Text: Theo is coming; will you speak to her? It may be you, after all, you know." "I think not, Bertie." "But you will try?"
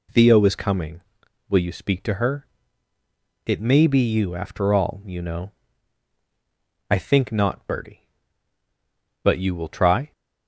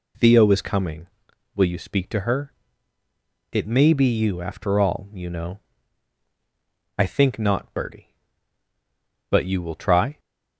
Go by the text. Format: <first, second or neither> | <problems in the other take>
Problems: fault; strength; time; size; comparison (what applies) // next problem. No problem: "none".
neither | none